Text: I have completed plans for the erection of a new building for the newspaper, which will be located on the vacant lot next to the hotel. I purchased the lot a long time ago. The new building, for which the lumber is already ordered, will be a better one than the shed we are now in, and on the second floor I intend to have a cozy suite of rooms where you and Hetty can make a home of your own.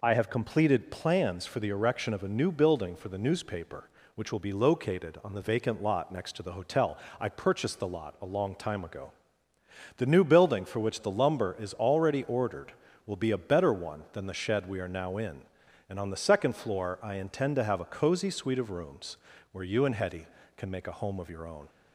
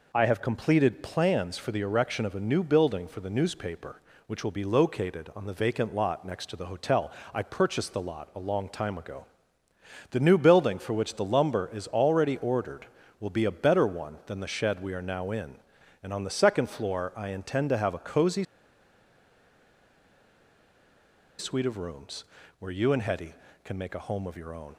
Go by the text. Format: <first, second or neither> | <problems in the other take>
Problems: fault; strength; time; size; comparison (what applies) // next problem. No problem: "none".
first | pauses between "cozy" and "suite"; strong; at 18.4 s; 2.9 s long // pauses between "rooms" and "where"; slight; at 22.2 s; 0.36 s long; slight in the first